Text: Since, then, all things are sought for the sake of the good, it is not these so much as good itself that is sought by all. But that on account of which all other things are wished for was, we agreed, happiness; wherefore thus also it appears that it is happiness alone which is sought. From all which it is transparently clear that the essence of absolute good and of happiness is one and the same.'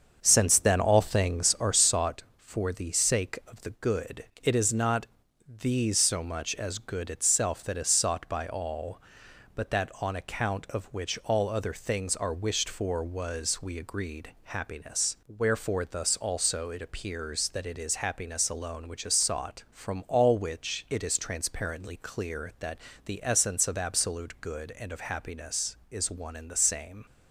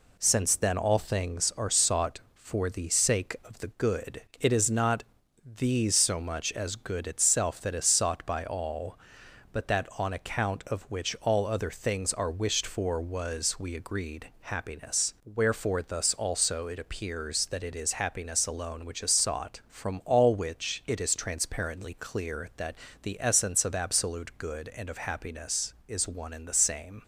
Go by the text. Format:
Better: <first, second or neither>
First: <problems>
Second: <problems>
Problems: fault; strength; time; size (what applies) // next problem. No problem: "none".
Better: second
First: starts louder than the rest; until 2.0 s; 7 dB // pauses between "not" and "these"; at 5.0 s; 0.40 s long // pauses between "that" and "the"; slight; at 22.7 s; 0.28 s long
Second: pauses between "not" and "these"; at 5.0 s; 0.40 s long // pauses between "that" and "the"; slight; at 22.7 s; 0.28 s long